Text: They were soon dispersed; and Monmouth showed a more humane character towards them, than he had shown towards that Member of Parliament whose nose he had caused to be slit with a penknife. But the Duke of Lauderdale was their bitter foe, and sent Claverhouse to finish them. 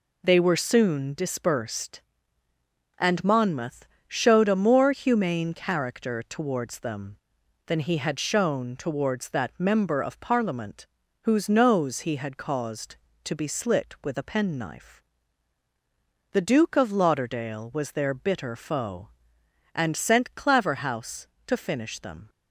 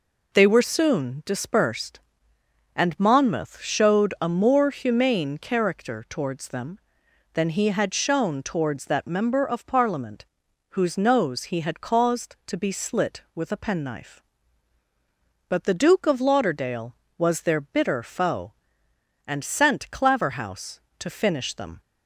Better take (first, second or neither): second